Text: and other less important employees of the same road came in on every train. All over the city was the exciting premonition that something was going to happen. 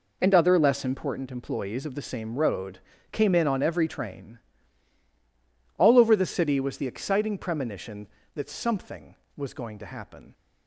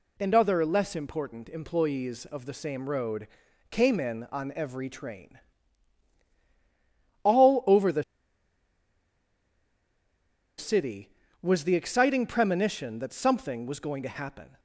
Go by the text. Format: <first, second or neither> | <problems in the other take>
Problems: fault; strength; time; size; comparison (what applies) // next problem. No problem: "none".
first | pauses between "road" and "came"; at 3.2 s; 0.44 s long; slight in the first // pauses between "the" and "city"; strong; at 8.0 s; 2.5 s long